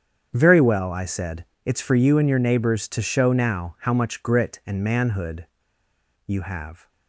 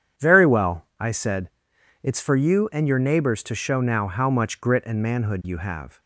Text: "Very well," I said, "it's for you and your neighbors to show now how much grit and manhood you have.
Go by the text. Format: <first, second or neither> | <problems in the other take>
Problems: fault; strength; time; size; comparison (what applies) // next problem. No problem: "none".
second | starts louder than the rest; strong; until 1.3 s; 8 dB; strong in the second // pauses between "manhood" and "you"; noticeable; at 5.4 s; 0.79 s long